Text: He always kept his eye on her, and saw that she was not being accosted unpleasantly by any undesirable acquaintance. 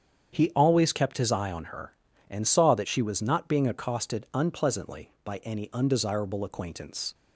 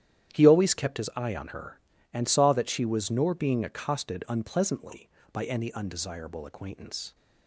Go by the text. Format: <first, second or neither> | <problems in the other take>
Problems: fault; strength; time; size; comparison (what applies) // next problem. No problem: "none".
first | starts louder than the rest; strong; until 1.4 s; 10.5 dB; strong in the first // says "nor" for "not"; at 3.1 s